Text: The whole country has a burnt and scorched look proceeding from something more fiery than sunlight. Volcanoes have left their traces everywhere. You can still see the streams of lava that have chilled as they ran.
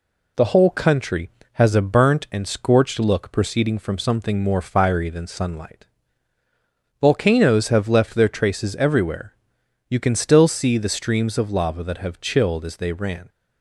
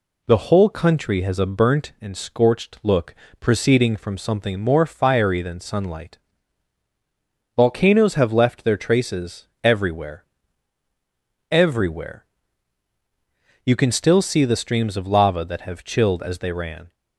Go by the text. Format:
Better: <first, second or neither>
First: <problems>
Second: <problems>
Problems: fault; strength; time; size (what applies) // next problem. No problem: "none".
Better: first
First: none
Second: pauses between "look" and "proceeding"; slight; at 3.1 s; 0.28 s long // pauses between "traces" and "everywhere"; slight; at 9.4 s; 0.16 s long // says "everywhere" twice; at 11.5 s